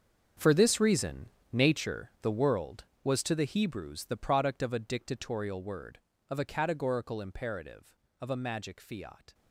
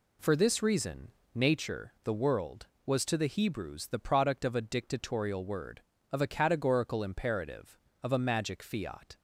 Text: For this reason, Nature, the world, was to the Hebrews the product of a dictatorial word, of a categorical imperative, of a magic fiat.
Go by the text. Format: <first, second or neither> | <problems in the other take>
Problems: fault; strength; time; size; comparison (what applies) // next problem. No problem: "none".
second | gets quieter; strong; throughout; 14 dB